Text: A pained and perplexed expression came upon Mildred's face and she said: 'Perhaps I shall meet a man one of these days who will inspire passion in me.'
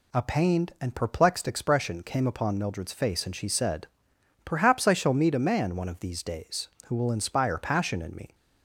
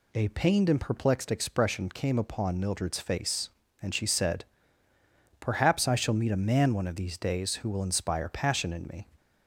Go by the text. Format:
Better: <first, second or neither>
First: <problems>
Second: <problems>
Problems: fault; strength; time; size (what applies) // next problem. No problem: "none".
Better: neither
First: none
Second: none